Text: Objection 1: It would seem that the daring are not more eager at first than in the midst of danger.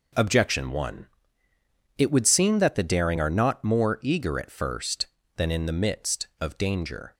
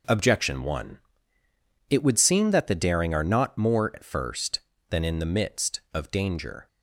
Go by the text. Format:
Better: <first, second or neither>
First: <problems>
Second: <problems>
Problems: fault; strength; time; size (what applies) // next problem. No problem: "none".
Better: first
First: none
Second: skips "eager"; at 3.9 s